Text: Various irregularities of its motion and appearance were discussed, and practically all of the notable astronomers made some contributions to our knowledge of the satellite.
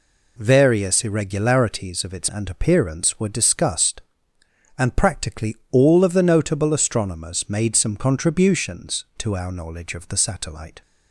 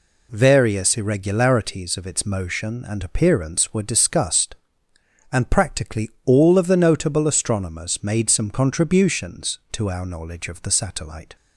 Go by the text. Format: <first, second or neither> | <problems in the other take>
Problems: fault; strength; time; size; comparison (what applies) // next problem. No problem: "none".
second | skips "motion"; at 2.2 s